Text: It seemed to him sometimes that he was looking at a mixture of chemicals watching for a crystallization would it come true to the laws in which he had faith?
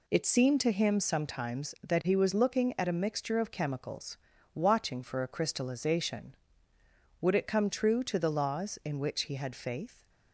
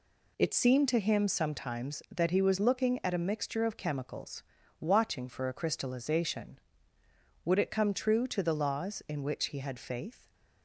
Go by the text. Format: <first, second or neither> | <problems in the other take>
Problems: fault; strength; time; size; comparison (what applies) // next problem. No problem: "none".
neither | pauses between "chemicals" and "watching"; the same in both